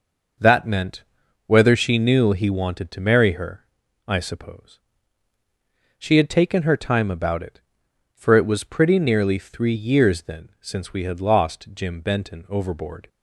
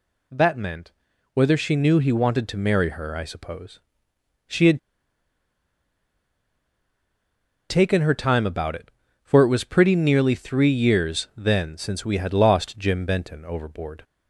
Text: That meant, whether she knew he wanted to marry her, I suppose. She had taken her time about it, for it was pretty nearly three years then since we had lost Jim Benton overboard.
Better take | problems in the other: first | pauses between "had" and "taken"; strong; at 4.7 s; 2.8 s long

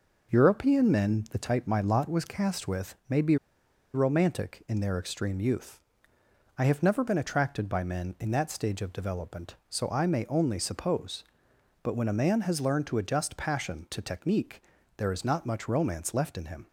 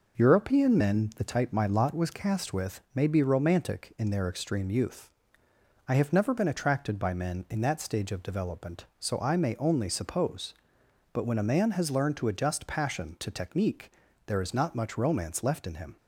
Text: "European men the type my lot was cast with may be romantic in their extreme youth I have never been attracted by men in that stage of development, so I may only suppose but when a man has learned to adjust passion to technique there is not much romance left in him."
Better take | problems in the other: second | pauses between "be" and "romantic"; noticeable; at 3.3 s; 0.58 s long // pauses between "youth" and "I"; noticeable; at 5.7 s; 0.80 s long; noticeable in the second // pauses between "technique" and "there"; slight; at 14.6 s; 0.36 s long; slight in the second

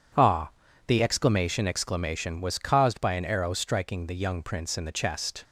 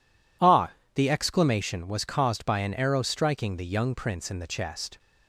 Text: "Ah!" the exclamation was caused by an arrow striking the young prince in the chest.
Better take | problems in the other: second | says "exclamation" twice; at 1.6 s

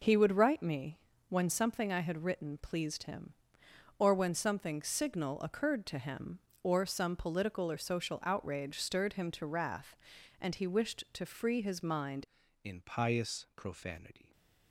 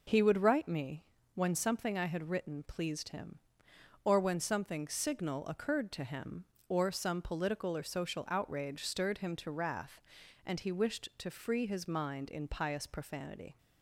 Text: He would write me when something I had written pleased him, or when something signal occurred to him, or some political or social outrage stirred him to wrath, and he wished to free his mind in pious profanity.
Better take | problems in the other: second | pauses between "me" and "when"; slight; at 0.9 s; 0.32 s long; slight in the second // changes voice at "in"; from 12.6 s on; 1.7 s long

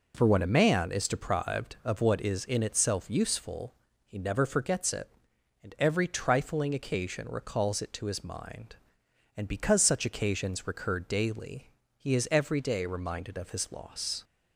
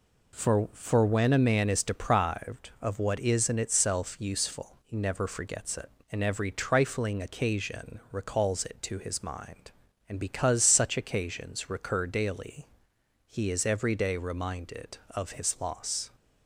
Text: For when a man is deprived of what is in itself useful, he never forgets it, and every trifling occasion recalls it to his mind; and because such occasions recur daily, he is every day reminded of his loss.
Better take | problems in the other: first | says "For" twice; at 0.7 s

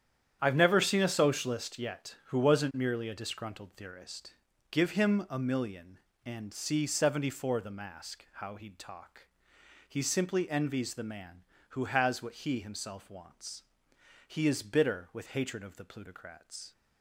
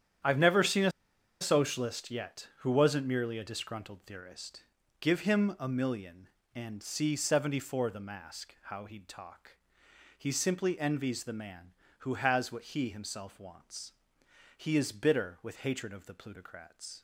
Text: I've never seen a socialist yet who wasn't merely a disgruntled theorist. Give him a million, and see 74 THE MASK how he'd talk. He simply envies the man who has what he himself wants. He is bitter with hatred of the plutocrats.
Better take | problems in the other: first | starts louder than the rest; strong; until 1.7 s; 9.5 dB; strong in the first // pauses between "a" and "socialist"; noticeable; at 0.9 s; 0.50 s long

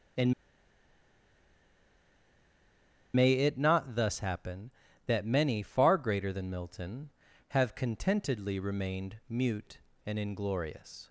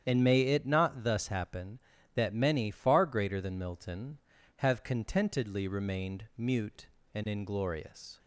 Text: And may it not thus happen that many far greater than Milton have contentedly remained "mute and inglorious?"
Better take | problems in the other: second | starts louder than the rest; strong; until 4.0 s; 9 dB; strong in the second // pauses between "And" and "may"; strong; at 0.3 s; 2.8 s long

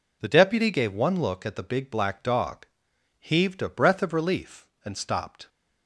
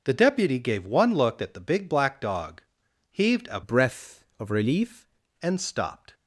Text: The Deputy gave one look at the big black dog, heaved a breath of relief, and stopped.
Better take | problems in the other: first | changes voice from "breath" to "relief"; from 3.6 to 5.0 s; 1.4 s long

